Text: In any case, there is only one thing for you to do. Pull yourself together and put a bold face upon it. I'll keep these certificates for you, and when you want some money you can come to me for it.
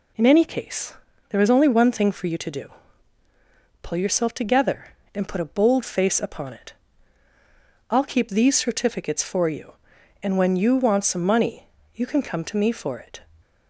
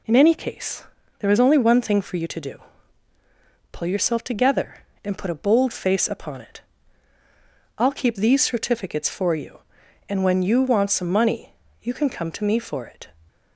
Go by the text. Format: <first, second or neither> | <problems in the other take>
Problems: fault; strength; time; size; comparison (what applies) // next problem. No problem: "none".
neither | pauses between "money" and "you"; slight; the same in both